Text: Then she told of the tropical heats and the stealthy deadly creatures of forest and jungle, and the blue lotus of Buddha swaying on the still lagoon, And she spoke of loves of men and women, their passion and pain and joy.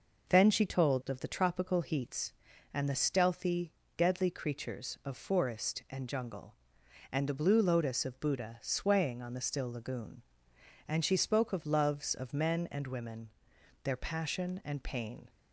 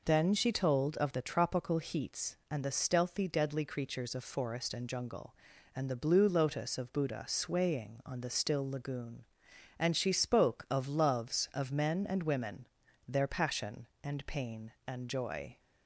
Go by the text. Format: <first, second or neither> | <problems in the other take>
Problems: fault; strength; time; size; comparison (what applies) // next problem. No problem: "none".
second | pauses between "stealthy" and "deadly"; slight; at 3.7 s; 0.26 s long // stops before "and joy"; at 15.2 s